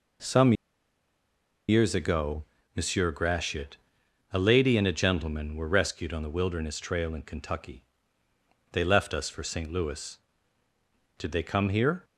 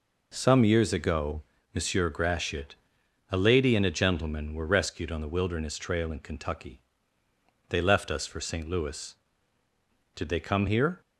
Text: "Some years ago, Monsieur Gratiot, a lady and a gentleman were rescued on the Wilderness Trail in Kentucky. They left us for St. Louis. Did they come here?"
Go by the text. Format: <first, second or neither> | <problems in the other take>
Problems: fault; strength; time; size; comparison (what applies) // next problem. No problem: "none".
second | pauses between "Some" and "years"; at 0.5 s; 1.1 s long